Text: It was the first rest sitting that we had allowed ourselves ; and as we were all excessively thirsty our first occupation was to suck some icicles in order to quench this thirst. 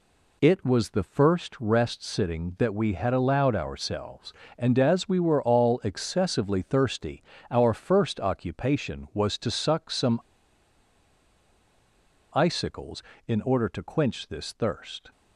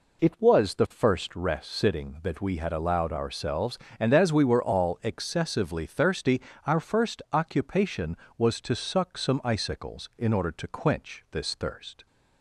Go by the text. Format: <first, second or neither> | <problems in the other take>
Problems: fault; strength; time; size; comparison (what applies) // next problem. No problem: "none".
second | pauses between "thirsty" and "our"; slight; at 7.2 s; 0.30 s long; slight in the second // pauses between "some" and "icicles"; strong; at 10.2 s; 2.1 s long